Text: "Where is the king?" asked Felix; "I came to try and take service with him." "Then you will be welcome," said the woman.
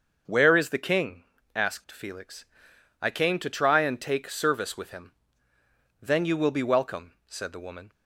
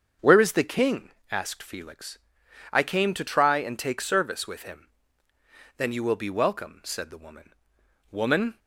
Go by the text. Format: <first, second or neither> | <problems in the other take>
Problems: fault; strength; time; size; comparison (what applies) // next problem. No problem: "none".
first | starts louder than the rest; until 1.4 s; 7 dB; also in the first // says "woman" twice; at 8.1 s